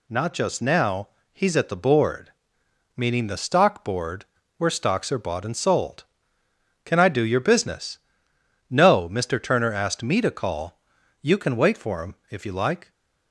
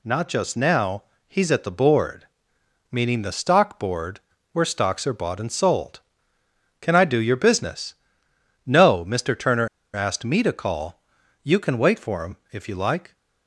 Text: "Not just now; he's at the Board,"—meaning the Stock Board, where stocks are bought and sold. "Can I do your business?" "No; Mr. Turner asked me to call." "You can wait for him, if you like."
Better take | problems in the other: first | pauses between "Turner" and "asked"; slight; at 9.6 s; 0.26 s long

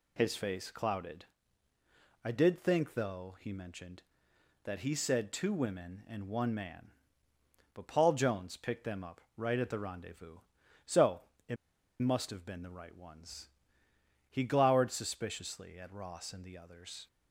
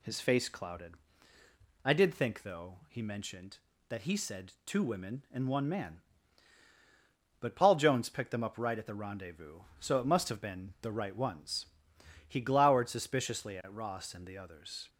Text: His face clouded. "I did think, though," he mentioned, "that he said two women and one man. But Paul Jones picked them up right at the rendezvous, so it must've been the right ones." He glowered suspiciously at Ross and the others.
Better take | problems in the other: second | pauses between "so" and "it"; slight; at 11.2 s; 0.26 s long // pauses between "it" and "must've"; noticeable; at 11.5 s; 0.46 s long

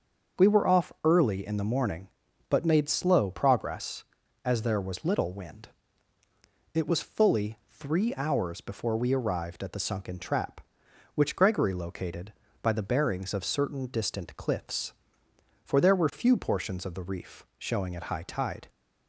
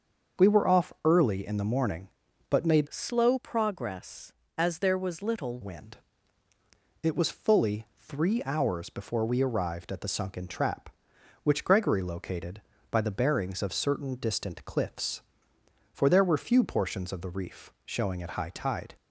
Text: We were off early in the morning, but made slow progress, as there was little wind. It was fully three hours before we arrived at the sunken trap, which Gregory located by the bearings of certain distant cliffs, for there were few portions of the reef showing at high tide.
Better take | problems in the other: first | starts louder than the rest; until 1.4 s; 6.5 dB; also in the first // changes voice from "slow" to "little"; from 2.8 to 5.5 s; 2.7 s long

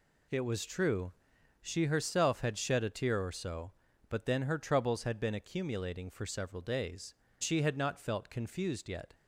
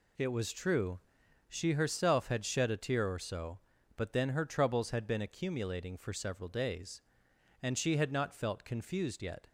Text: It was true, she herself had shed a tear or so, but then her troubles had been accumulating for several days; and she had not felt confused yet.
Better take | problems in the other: second | skips "and"; at 7.2 s

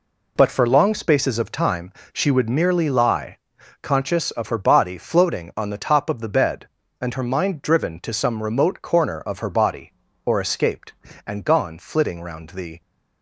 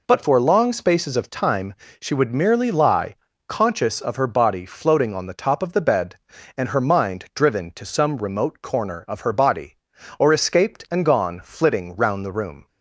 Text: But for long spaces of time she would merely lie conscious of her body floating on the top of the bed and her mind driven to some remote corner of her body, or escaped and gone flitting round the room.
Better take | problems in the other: second | pauses between "time" and "she"; slight; at 1.9 s; 0.22 s long; slight in the second // pauses between "lie" and "conscious"; at 3.3 s; 0.42 s long; slight in the second // stops before "room"; at 12.8 s

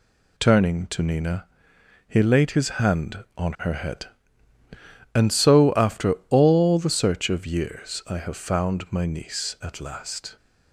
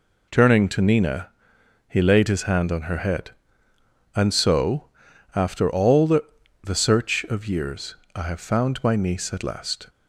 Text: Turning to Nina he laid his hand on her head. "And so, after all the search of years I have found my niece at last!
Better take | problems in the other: first | pauses between "Nina" and "he"; noticeable; at 1.2 s; 0.60 s long; noticeable in the first // says "the" twice; at 6.6 s // pauses between "years" and "I"; slight; at 7.9 s; 0.18 s long

